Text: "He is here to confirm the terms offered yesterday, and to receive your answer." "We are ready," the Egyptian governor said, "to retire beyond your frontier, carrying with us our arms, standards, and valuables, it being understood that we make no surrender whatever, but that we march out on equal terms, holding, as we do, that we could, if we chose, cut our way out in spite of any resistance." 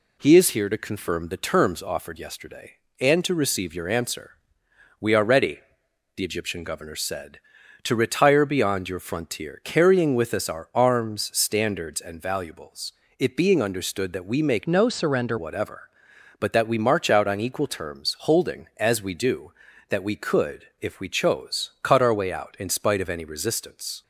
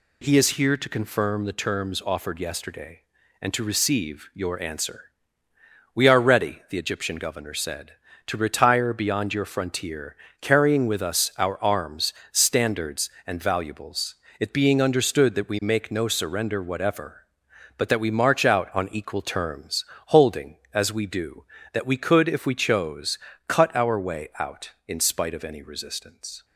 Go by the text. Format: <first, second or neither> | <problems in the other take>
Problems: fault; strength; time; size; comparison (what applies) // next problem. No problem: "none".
second | changes voice from "no" to "surrender"; from 14.6 to 15.3 s; 0.7 s long